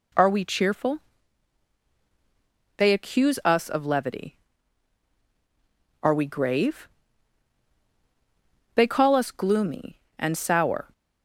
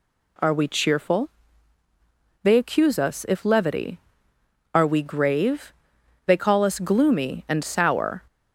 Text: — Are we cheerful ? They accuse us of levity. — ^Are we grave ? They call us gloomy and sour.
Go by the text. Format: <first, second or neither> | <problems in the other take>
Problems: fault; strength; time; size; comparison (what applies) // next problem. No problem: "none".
first | says "if" for "of"; at 3.2 s